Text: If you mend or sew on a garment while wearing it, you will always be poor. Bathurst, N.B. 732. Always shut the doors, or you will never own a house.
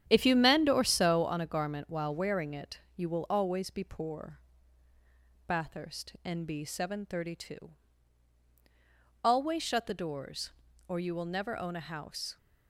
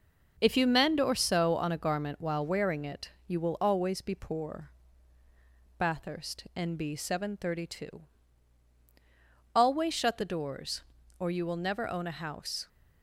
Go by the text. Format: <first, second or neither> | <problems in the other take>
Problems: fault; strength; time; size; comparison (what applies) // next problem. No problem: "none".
second | starts louder than the rest; strong; until 1.3 s; 9.5 dB